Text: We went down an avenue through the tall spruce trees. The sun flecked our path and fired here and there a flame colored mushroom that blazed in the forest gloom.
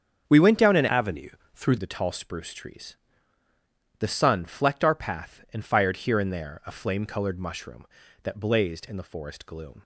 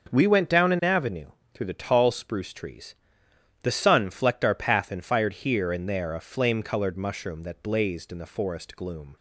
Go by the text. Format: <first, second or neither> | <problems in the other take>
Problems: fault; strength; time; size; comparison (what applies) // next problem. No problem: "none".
second | starts louder than the rest; strong; until 1.3 s; 7 dB; also in the second // changes voice from "avenue" to "through"; from 0.8 to 1.7 s; 0.9 s long // pauses between "avenue" and "through"; slight; at 1.3 s; 0.24 s long; slight in the second